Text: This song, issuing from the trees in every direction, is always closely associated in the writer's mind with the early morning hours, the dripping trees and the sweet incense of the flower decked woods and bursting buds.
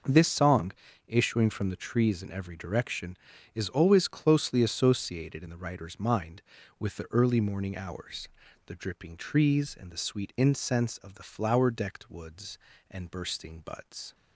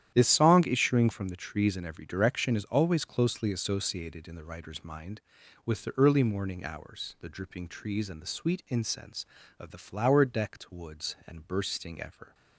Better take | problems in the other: first | starts louder than the rest; strong; until 1.1 s; 10.5 dB // says "ever" for "buds"; at 12.0 s

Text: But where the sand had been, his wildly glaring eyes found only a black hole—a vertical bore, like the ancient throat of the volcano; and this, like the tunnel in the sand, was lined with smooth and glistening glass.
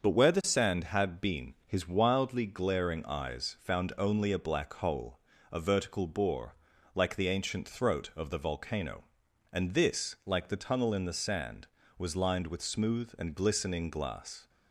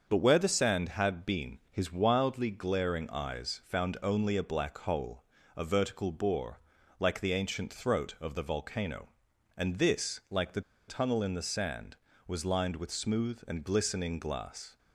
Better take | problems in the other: first | starts louder than the rest; until 1.1 s; 6.5 dB; also in the first // pauses between "the" and "tunnel"; slight; at 10.6 s; 0.26 s long

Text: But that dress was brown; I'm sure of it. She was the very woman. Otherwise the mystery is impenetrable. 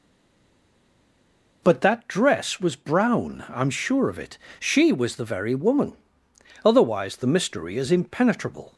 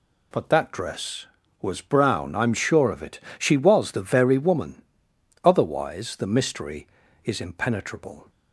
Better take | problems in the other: second | stays silent before the first word; noticeable; until 1.6 s; 1.6 s long

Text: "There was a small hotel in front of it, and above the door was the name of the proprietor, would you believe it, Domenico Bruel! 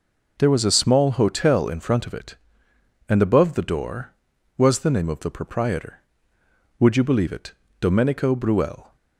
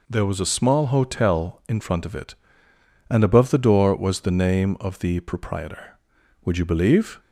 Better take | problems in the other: first | stops before "it Domenico Bruel"; at 7.1 s

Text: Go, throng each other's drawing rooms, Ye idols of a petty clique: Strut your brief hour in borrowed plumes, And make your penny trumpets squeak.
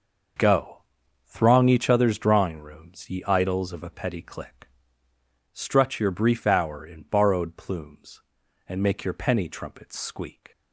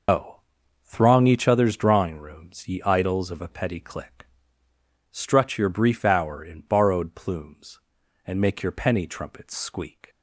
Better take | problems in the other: first | loses the start of "Go"; at 0.0 s; 140 ms

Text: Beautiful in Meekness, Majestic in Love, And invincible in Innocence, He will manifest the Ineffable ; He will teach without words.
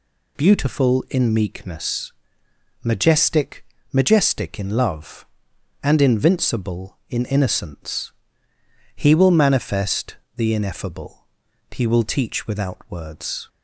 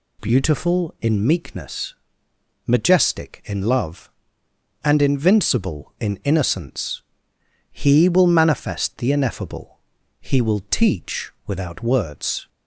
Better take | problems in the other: second | says "Majestic" twice; at 3.9 s // pauses between "manifest" and "the"; slight; at 10.1 s; 0.20 s long

